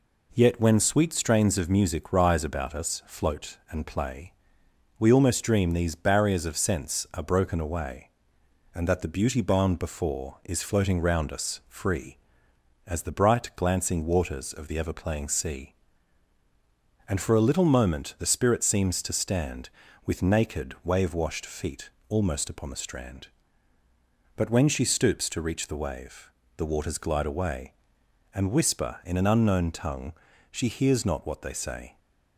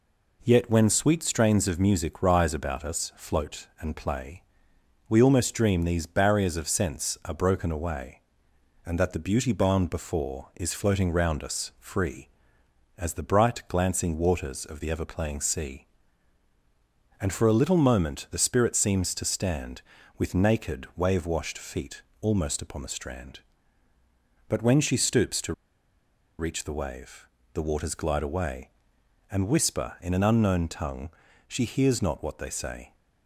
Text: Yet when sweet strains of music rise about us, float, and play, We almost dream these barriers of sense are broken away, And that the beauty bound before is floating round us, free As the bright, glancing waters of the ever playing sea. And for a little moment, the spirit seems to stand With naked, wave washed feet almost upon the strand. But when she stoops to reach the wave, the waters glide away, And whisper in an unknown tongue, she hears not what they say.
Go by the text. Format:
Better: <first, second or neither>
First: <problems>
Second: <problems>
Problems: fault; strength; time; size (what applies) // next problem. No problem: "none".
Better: first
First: pauses between "feet" and "almost"; slight; at 21.8 s; 0.22 s long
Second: pauses between "feet" and "almost"; slight; at 22.0 s; 0.22 s long // pauses between "to" and "reach"; noticeable; at 25.5 s; 0.86 s long